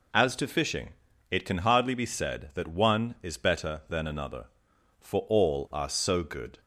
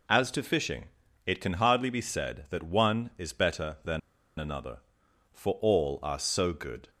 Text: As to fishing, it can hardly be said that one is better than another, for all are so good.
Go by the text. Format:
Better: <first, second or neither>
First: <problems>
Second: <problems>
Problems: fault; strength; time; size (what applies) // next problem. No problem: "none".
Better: first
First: none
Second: pauses between "than" and "another"; at 3.9 s; 0.39 s long